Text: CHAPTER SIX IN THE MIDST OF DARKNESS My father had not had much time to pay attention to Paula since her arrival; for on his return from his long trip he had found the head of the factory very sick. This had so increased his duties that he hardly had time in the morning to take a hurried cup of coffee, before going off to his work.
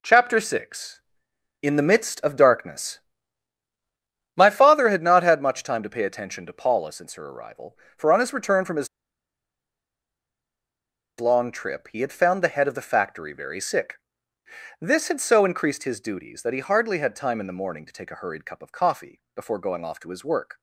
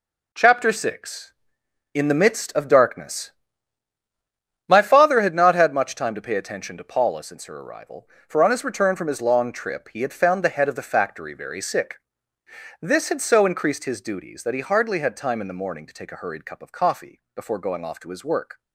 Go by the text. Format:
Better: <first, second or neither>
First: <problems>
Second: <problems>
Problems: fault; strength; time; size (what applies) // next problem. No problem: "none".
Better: second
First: pauses between "DARKNESS" and "My"; strong; at 3.0 s; 1.3 s long // pauses between "his" and "long"; strong; at 8.8 s; 2.3 s long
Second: pauses between "DARKNESS" and "My"; strong; at 3.3 s; 1.3 s long